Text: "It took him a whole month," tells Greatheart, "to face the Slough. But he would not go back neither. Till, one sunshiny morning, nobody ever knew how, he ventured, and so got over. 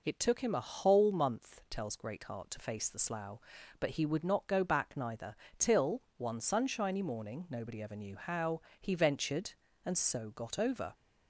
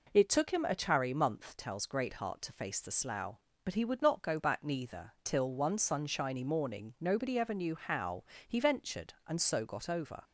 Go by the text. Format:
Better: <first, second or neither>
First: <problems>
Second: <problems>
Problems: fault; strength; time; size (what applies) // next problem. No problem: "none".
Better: first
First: none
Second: says "chary" for "whole"; at 0.7 s